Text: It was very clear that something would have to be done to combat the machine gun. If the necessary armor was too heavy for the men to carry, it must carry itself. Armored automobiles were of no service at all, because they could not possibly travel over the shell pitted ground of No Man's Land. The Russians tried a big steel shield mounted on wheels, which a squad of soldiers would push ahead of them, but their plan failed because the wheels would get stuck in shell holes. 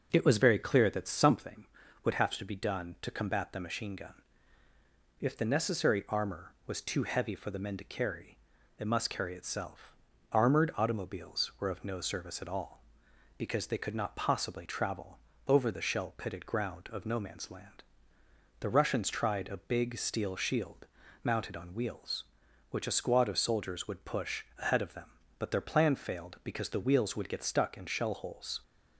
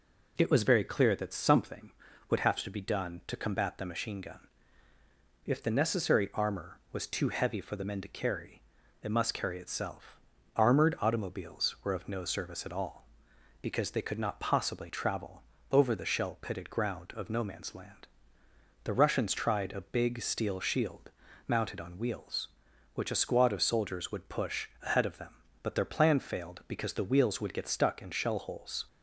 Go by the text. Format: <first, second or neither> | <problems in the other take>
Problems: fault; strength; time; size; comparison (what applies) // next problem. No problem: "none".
second | starts louder than the rest; noticeable; until 1.3 s; 6 dB // pauses between "travel" and "over"; slight; at 15.1 s; 0.30 s long; slight in the second // pauses between "shield" and "mounted"; slight; at 20.8 s; 0.36 s long; slight in the second // pauses between "push" and "ahead"; slight; at 24.4 s; 0.16 s long; slight in the second